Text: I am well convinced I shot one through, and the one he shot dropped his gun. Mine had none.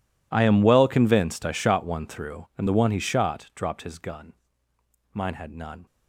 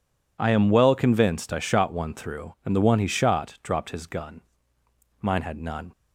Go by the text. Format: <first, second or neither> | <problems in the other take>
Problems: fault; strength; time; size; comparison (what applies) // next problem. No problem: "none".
second | gets quieter; strong; throughout; 21 dB